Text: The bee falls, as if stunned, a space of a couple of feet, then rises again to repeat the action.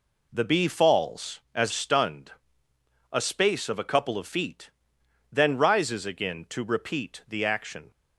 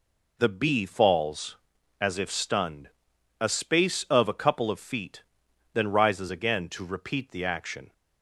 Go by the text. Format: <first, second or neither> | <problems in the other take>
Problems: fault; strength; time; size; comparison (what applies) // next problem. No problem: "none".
second | skips "if"; at 1.7 s